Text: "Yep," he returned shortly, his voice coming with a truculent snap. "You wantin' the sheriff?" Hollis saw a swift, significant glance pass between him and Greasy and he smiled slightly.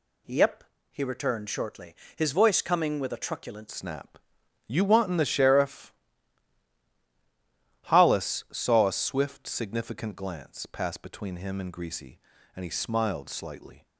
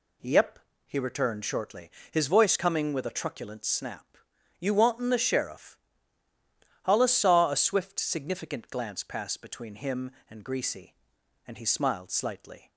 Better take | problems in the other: second | changes voice at "snap"; from 3.6 s on; 10.2 s long

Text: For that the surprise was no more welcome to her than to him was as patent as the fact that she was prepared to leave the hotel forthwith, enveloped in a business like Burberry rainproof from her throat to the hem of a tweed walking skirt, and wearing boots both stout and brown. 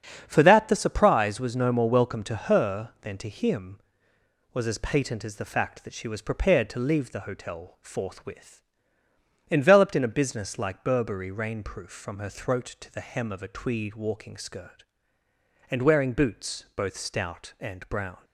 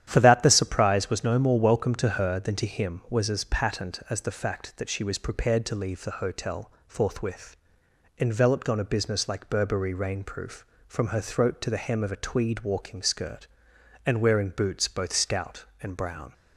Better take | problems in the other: first | starts louder than the rest; strong; until 1.0 s; 10.5 dB; strong in the first // pauses between "hotel" and "forthwith"; slight; at 6.7 s; 0.16 s long // says "on" for "in"; at 8.6 s

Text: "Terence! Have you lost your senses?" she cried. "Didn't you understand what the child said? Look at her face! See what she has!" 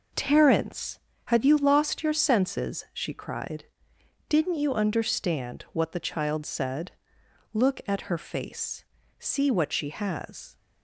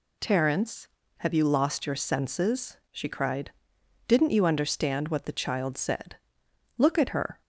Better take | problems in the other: first | stops before "face See what she has"; at 7.4 s

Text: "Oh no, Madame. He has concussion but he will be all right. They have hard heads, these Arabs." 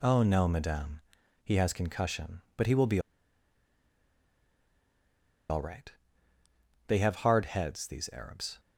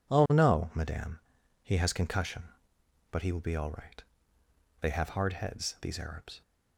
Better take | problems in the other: second | pauses between "be" and "all"; strong; at 2.9 s; 2.5 s long

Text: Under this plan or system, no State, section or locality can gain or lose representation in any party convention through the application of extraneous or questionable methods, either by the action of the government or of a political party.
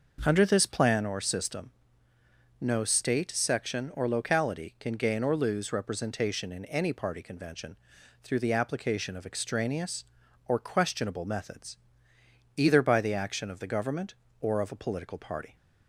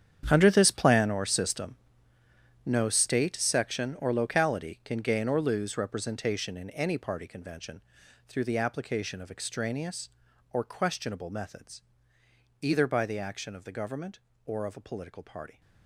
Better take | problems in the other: first | gets quieter; strong; throughout; 14.5 dB // pauses between "convention" and "through"; at 7.8 s; 0.44 s long; also in the first

